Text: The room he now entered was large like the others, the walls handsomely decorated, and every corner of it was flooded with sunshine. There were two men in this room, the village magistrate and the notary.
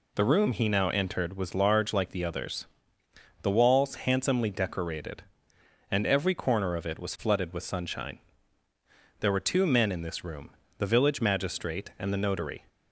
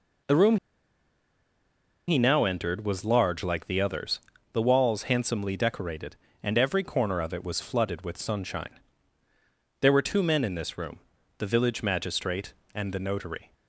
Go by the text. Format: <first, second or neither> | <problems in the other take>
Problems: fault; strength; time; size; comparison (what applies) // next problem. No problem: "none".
first | pauses between "room" and "he"; strong; at 0.5 s; 1.5 s long